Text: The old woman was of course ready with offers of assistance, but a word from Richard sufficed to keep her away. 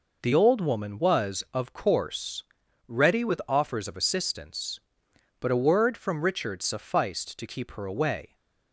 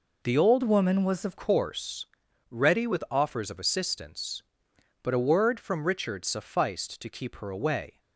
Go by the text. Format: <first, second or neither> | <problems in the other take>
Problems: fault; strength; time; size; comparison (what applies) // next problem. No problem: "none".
first | changes voice from "woman" to "of"; from 0.6 to 1.3 s; 0.7 s long // pauses between "course" and "ready"; noticeable; at 2.0 s; 0.46 s long; noticeable in the first